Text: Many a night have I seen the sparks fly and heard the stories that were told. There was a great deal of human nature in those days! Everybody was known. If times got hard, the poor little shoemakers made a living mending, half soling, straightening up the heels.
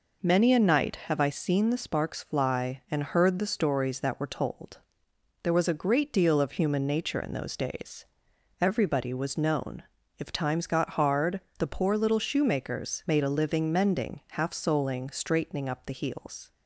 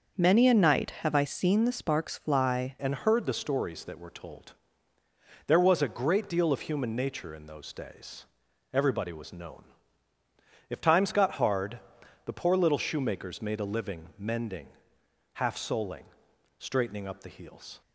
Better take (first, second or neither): first